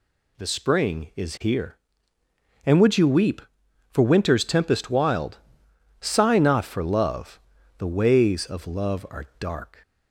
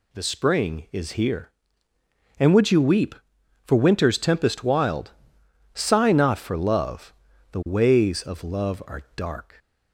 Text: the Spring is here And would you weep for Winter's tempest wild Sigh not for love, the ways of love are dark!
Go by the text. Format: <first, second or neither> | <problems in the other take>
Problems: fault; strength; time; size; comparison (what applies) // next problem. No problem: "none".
neither | pauses between "wild" and "Sigh"; noticeable; the same in both